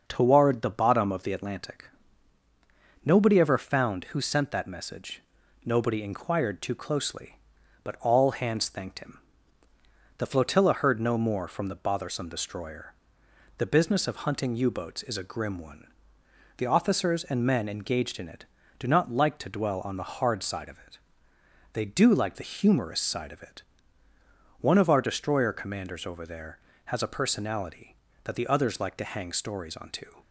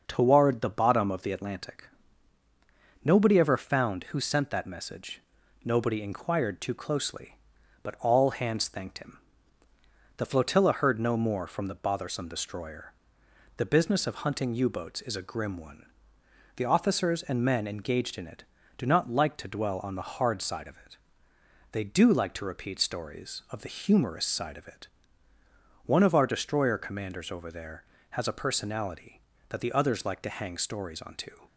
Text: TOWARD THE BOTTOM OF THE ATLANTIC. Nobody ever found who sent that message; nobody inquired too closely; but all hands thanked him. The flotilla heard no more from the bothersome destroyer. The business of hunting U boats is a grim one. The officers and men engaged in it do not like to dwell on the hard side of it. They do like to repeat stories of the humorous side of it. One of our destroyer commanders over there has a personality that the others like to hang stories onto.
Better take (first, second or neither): second